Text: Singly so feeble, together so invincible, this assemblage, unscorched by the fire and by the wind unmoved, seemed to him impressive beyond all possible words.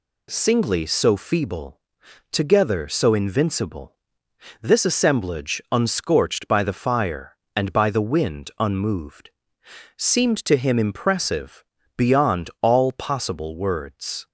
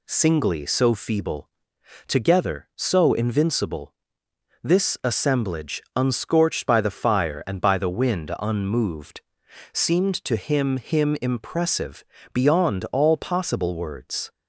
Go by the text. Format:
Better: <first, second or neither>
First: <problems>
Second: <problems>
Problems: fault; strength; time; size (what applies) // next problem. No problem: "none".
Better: first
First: pauses between "impressive" and "beyond"; slight; at 11.6 s; 0.34 s long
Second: says "him" twice; at 10.7 s // pauses between "impressive" and "beyond"; slight; at 12.0 s; 0.28 s long